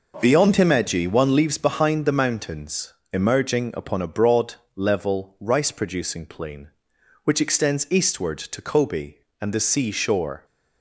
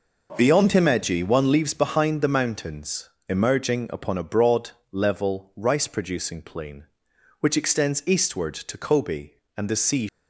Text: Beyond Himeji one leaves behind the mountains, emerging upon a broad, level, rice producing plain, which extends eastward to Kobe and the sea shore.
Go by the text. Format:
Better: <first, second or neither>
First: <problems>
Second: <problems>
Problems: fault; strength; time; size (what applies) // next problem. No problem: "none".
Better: first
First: none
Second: stops before "shore"; at 10.0 s